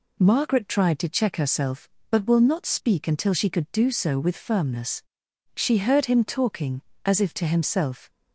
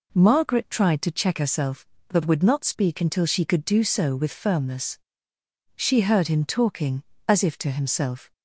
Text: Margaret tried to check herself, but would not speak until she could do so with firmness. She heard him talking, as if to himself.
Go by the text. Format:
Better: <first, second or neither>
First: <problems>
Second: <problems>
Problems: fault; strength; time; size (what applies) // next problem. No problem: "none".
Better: second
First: says "will" for "would"; at 2.2 s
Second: none